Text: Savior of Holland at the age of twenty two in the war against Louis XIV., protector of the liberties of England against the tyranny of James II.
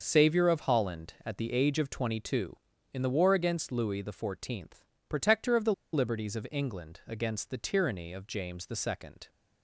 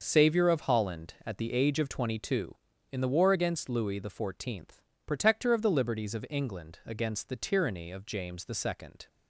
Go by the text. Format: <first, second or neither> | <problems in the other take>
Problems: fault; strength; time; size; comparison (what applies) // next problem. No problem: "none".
second | starts louder than the rest; noticeable; until 1.0 s; 6 dB; also in the second // pauses between "the" and "liberties"; slight; at 5.7 s; 0.21 s long